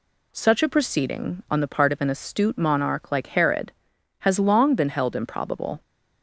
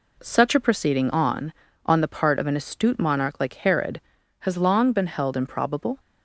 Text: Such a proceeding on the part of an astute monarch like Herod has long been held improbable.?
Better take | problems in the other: first | says "on" twice; at 1.8 s

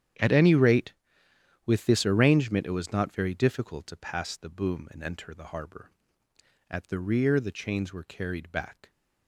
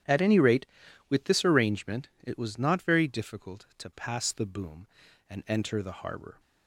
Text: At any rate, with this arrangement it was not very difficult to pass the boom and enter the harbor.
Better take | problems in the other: second | starts louder than the rest; strong; until 1.9 s; 10 dB; strong in the second // goes on to say "At the rear the chains were carried back"; strong; from 6.6 s on; 2.2 s long

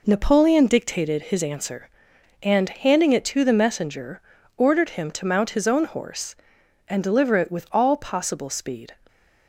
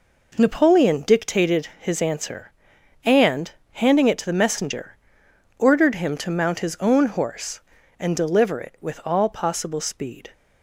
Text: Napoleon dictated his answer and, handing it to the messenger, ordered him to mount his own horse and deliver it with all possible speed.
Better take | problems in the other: neither | none

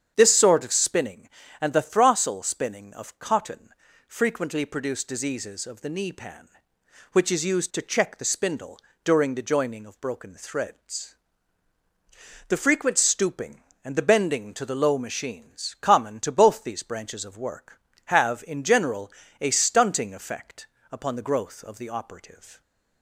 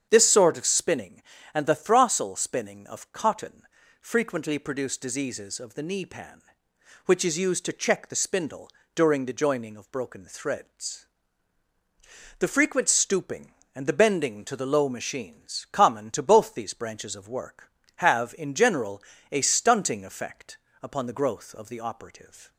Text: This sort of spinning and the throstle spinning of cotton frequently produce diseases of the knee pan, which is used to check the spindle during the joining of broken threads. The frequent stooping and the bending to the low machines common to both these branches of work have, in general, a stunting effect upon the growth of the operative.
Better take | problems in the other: neither | starts louder than the rest; strong; the same in both // pauses between "cotton" and "frequently"; the same in both // pauses between "spindle" and "during"; slight; the same in both // pauses between "effect" and "upon"; slight; the same in both

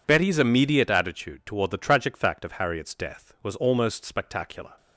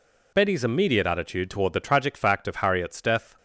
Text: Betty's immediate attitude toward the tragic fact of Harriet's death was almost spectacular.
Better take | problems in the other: first | stops before "was almost spectacular"; at 3.3 s

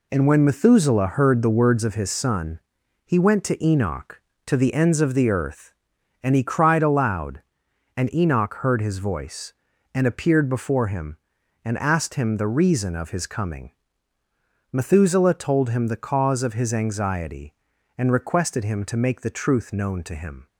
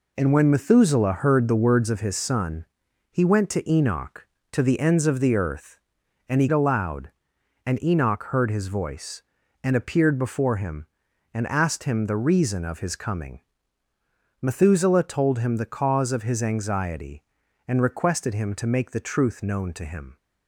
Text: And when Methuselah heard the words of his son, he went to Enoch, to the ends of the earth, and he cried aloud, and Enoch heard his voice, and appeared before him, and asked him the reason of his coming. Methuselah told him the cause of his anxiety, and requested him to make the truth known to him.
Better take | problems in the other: first | skips "cried"; at 6.4 s

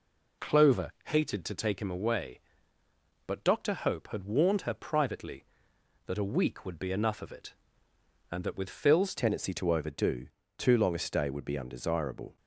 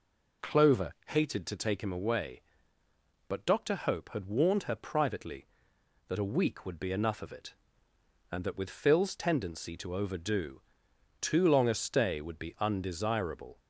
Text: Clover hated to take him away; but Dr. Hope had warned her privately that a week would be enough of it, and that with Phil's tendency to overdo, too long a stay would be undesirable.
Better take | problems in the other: second | changes voice at "tendency"; from 9.1 s on; 3.2 s long

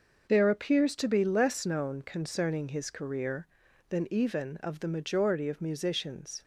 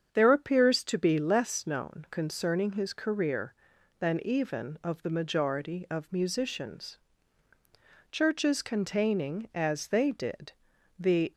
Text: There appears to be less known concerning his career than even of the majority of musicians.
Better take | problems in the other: first | starts louder than the rest; strong; until 1.1 s; 7.5 dB; noticeable in the first // goes on to say "Churches containing as they did the"; strong; from 8.1 s on; 3.2 s long

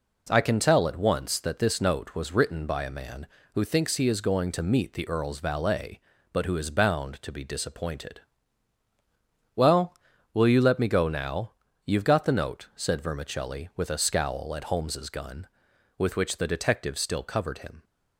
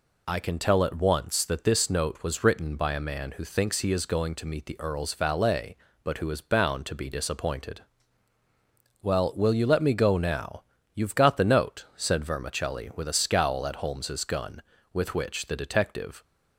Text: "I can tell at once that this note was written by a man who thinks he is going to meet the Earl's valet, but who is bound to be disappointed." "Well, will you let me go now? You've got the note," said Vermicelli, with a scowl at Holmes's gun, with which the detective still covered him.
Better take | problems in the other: first | stops before "still covered him"; at 16.2 s

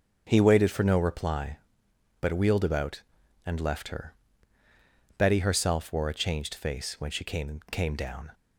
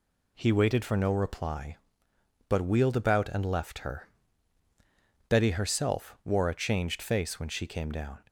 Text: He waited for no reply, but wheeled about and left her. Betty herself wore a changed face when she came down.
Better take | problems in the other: second | starts louder than the rest; until 1.2 s; 6.5 dB // says "came" twice; at 7.7 s

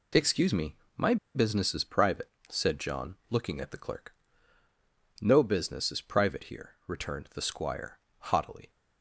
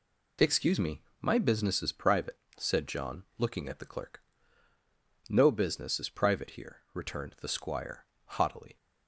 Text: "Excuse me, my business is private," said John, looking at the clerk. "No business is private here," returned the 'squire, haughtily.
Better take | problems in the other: second | pauses between "my" and "business"; slight; at 1.1 s; 0.19 s long

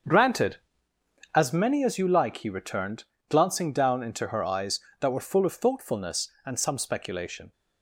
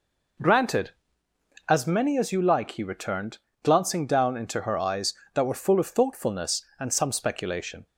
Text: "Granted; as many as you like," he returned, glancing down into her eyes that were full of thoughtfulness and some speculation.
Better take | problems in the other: second | gets quieter; strong; throughout; 10.5 dB

